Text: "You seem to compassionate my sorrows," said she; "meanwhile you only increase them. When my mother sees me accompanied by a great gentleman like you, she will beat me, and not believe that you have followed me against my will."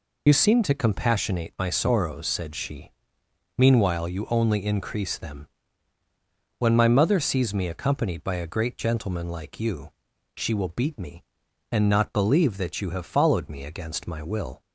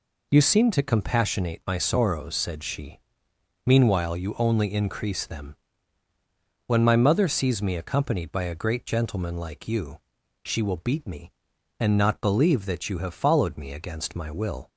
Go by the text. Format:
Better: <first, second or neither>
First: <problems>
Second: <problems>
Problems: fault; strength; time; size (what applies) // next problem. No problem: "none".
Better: second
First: loses the start of "You"; at 0.2 s; 45 ms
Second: none